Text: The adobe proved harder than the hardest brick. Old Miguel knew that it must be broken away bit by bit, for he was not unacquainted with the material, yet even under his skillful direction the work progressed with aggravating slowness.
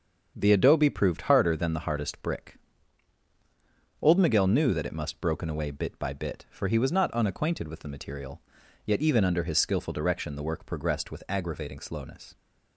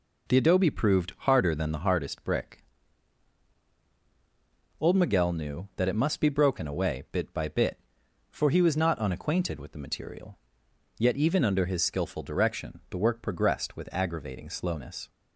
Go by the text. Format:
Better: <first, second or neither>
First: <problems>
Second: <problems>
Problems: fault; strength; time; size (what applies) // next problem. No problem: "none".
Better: second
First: starts louder than the rest; until 1.3 s; 7 dB // skips "be"; at 5.1 s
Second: none